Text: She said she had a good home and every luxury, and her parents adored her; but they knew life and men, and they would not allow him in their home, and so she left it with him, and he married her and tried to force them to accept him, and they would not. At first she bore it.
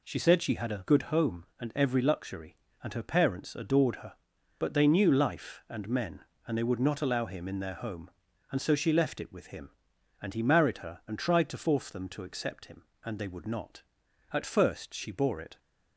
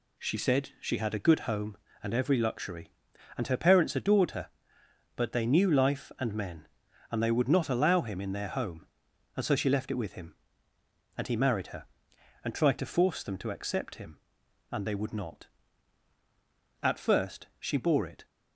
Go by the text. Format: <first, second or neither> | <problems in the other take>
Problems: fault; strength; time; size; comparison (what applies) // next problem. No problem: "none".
neither | none